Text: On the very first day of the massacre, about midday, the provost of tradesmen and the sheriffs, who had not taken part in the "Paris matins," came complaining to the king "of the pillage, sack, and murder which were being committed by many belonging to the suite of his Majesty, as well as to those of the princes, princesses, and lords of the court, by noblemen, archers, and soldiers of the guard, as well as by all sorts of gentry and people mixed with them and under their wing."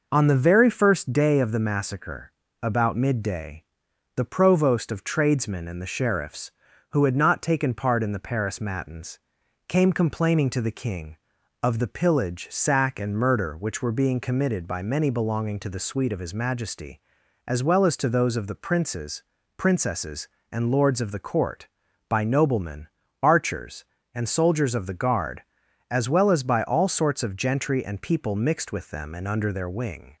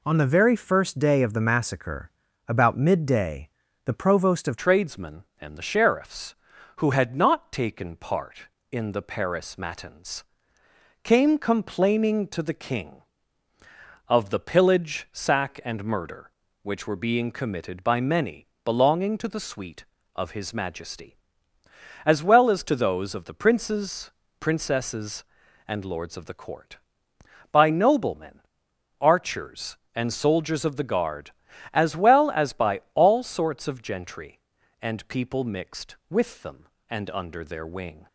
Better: first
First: none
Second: changes voice at "tradesmen"; from 4.5 s on; 33.5 s long // pauses between "many" and "belonging"; slight; at 18.4 s; 0.18 s long

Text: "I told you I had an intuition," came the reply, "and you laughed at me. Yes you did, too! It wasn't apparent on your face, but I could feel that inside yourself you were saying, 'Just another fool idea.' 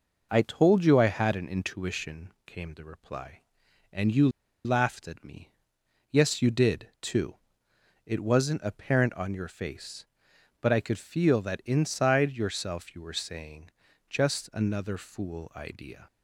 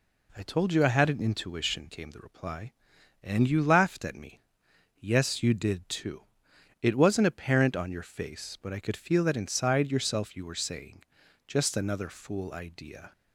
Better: second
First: pauses between "you" and "laughed"; slight; at 4.2 s; 0.35 s long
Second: none

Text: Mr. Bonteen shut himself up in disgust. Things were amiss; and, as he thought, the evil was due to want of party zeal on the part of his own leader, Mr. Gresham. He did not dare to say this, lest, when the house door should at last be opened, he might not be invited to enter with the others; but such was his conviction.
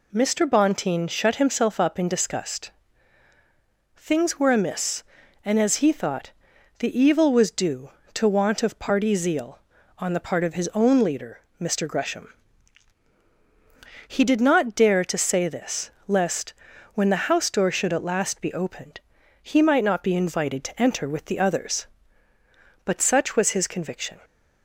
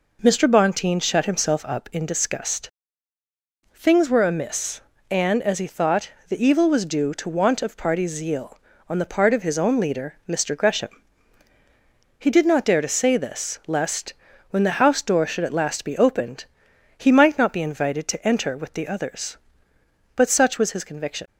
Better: neither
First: none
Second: none

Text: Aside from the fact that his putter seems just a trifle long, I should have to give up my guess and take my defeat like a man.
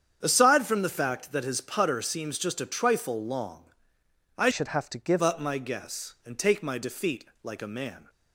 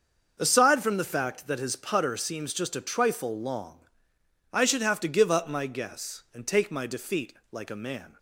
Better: second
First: starts louder than the rest; strong; until 1.2 s; 8 dB // changes voice from "should" to "give"; from 4.5 to 5.2 s; 0.7 s long // pauses between "defeat" and "like"; slight; at 7.2 s; 0.20 s long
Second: starts louder than the rest; until 1.4 s; 6.5 dB // pauses between "defeat" and "like"; slight; at 7.3 s; 0.20 s long

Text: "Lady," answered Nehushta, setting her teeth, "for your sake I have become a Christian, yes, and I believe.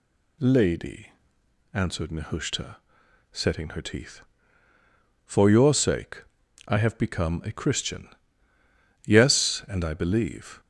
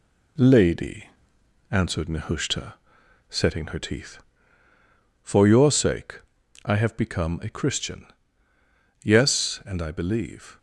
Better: first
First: pauses between "sake" and "I"; at 6.2 s; 0.44 s long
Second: gets quieter; slight; throughout; 3.5 dB // pauses between "sake" and "I"; at 6.2 s; 0.44 s long

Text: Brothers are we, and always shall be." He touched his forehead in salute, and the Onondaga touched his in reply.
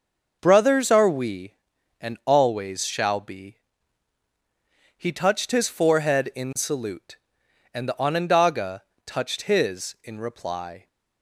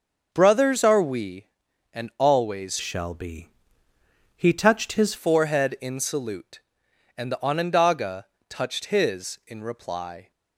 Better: first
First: pauses between "Onondaga" and "touched"; slight; at 8.8 s; 0.24 s long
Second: starts louder than the rest; until 1.3 s; 6.5 dB // changes voice from "shall" to "his"; from 2.8 to 5.1 s; 2.3 s long // pauses between "Onondaga" and "touched"; slight; at 8.2 s; 0.24 s long

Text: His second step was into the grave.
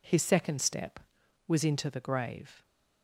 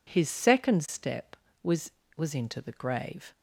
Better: first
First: none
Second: says "was" twice; at 2.1 s

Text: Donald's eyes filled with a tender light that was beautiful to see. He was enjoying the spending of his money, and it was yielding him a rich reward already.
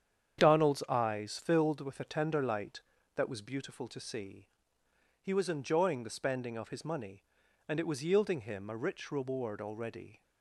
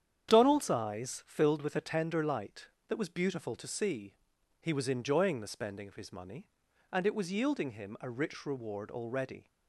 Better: neither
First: starts louder than the rest; strong; until 1.4 s; 8.5 dB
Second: starts louder than the rest; strong; until 1.3 s; 9 dB

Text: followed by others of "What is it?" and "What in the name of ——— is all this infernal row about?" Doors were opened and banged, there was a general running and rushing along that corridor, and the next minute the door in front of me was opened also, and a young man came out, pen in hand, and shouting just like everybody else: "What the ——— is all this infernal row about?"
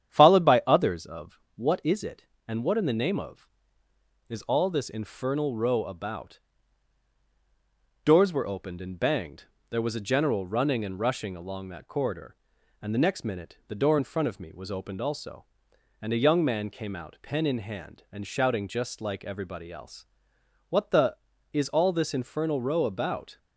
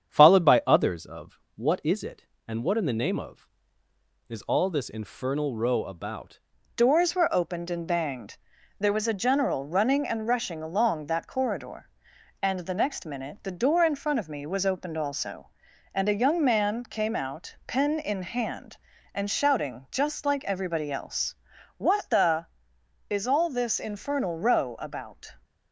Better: first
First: starts louder than the rest; strong; until 1.1 s; 9 dB // pauses between "of" and "What"; slight; at 1.3 s; 0.16 s long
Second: starts louder than the rest; strong; until 1.1 s; 8 dB // pauses between "of" and "What"; slight; at 1.3 s; 0.16 s long // changes voice at "Doors"; from 6.7 s on; 18.6 s long

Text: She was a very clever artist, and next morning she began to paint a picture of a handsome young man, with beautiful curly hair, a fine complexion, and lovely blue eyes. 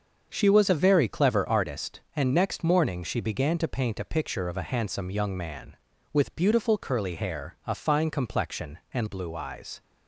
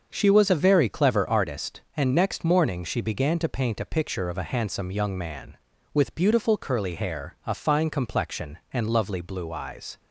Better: second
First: starts louder than the rest; until 1.3 s; 6.5 dB // skips "lovely"; at 9.0 s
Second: starts louder than the rest; until 1.1 s; 6.5 dB

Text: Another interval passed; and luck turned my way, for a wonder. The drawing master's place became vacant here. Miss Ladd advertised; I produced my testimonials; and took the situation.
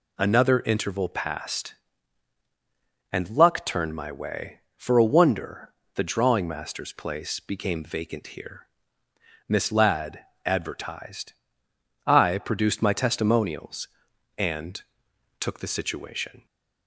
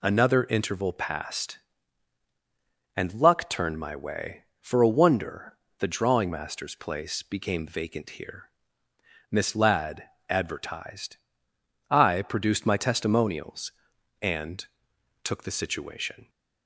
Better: neither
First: pauses between "Ladd" and "advertised"; slight; at 10.1 s; 0.26 s long // pauses between "and" and "took"; noticeable; at 14.8 s; 0.60 s long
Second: pauses between "Ladd" and "advertised"; slight; at 10.0 s; 0.26 s long // pauses between "and" and "took"; noticeable; at 14.6 s; 0.60 s long

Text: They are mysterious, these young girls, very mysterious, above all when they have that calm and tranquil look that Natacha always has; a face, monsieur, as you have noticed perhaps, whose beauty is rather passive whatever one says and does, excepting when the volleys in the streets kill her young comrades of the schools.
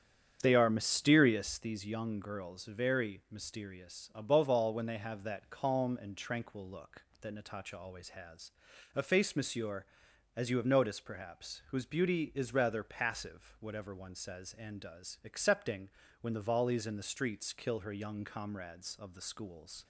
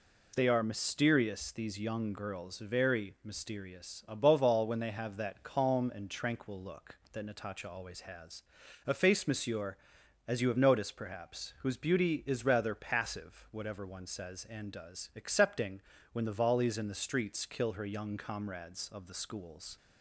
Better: second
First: starts louder than the rest; strong; until 1.8 s; 8 dB // pauses between "excepting" and "when"; slight; at 15.9 s; 0.32 s long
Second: pauses between "excepting" and "when"; slight; at 15.8 s; 0.32 s long

